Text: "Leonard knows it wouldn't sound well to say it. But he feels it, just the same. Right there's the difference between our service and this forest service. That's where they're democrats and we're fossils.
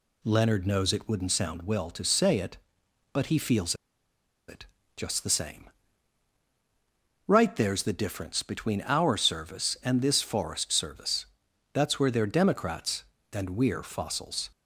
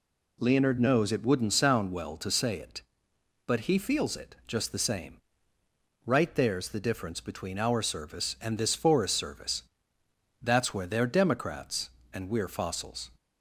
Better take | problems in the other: second | pauses between "feels" and "it"; noticeable; at 3.7 s; 0.74 s long

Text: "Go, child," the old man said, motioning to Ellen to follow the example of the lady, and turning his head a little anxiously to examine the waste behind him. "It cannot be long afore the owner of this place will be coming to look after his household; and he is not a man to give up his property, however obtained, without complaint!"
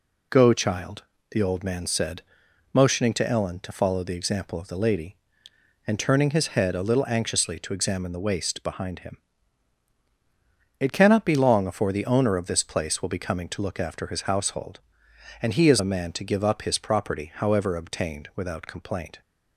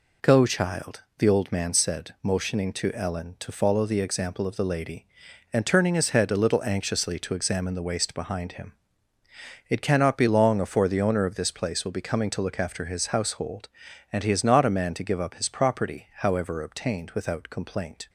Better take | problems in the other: second | skips "not"; at 15.8 s

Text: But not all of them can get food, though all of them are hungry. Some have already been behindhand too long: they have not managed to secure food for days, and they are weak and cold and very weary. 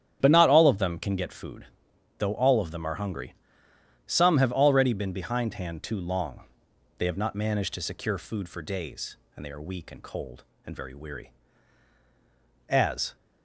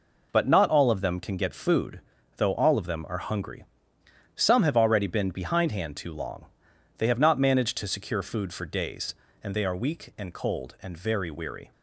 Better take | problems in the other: second | starts louder than the rest; strong; until 1.2 s; 9.5 dB // goes on to say "As"; slight; from 12.6 s on; 0.46 s long

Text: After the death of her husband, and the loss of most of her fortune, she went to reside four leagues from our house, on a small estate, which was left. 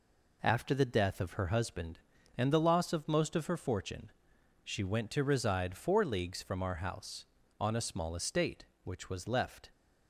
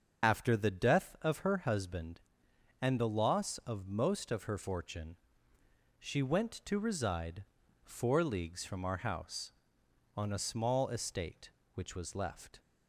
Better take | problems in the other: first | loses the start of "After"; at 0.2 s; 55 ms // starts louder than the rest; until 1.3 s; 6.5 dB // pauses between "reside" and "four"; at 7.4 s; 0.40 s long

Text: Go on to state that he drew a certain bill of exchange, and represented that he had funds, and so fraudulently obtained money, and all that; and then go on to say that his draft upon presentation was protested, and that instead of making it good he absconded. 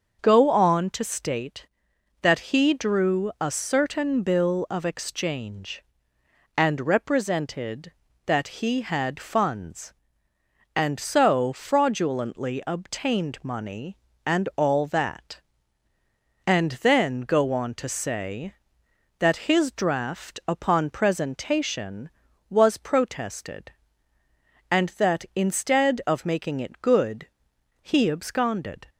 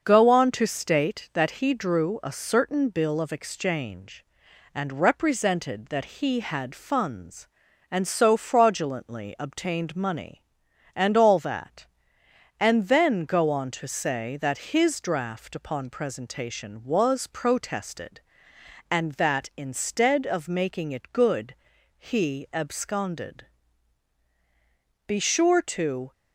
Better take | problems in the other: first | starts louder than the rest; until 1.0 s; 6.5 dB; also in the first // pauses between "good" and "he"; at 21.5 s; 0.44 s long; noticeable in the first // goes on to say "Be sure to"; noticeable; from 25.0 s on; 1.0 s long

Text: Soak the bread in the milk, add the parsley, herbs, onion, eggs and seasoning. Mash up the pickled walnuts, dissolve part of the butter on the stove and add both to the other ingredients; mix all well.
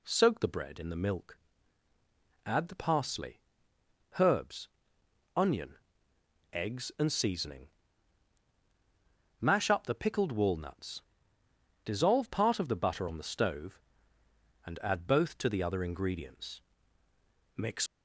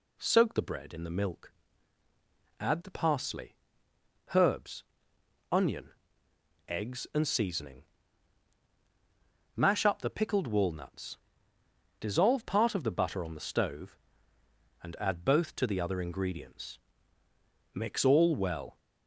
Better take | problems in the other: second | stops before "all well"; at 17.8 s

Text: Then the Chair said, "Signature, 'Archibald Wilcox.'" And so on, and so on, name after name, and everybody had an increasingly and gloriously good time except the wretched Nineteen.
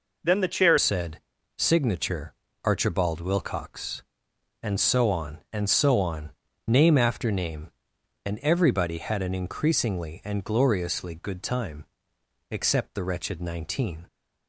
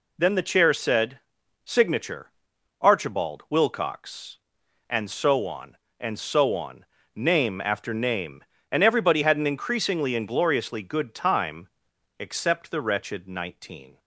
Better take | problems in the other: second | changes voice at "said"; from 0.7 s on; 13.3 s long // pauses between "time" and "except"; noticeable; at 11.8 s; 0.66 s long; noticeable in the second

